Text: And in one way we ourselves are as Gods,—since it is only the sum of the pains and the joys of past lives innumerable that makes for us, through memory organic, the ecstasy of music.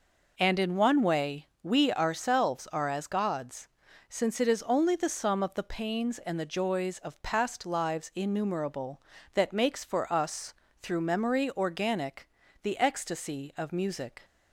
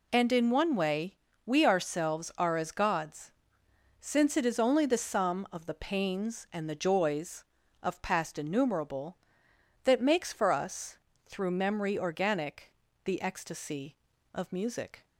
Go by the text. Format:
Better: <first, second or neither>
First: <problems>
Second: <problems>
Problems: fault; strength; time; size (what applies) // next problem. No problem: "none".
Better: first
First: pauses between "way" and "we"; slight; at 1.4 s; 0.16 s long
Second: pauses between "way" and "we"; slight; at 1.1 s; 0.30 s long // skips "lives"; at 8.3 s